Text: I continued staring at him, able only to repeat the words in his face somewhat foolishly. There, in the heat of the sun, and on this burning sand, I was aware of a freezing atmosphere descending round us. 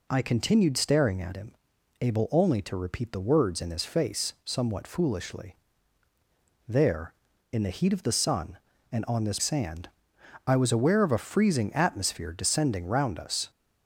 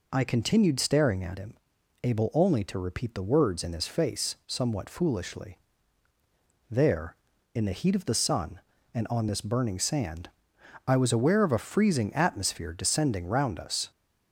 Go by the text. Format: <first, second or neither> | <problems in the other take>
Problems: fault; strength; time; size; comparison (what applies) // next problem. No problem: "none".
second | skips "burning"; at 9.3 s